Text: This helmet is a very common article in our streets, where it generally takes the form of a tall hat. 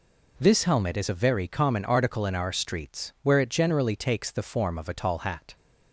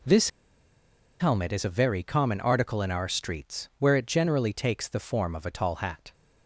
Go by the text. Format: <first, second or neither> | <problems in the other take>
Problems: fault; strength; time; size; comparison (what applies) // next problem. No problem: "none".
first | pauses between "This" and "helmet"; noticeable; at 0.2 s; 0.90 s long